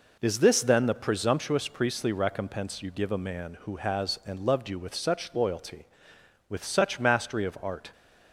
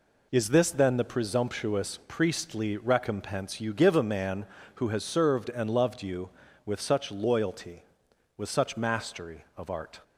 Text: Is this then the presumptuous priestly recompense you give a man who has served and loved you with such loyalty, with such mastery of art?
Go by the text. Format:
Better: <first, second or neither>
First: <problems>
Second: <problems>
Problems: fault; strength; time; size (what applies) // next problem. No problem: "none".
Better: second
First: skips "served"; at 4.2 s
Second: none